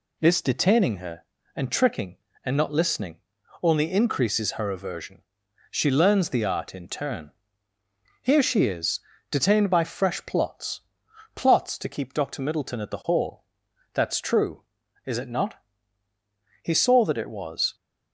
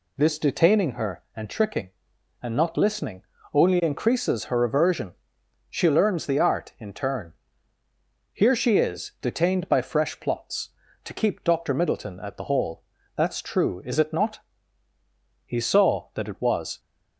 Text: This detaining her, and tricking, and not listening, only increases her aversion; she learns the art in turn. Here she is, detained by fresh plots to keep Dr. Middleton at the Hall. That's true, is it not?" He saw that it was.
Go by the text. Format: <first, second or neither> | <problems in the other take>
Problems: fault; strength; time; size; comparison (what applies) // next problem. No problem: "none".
second | says "plots" twice; at 11.3 s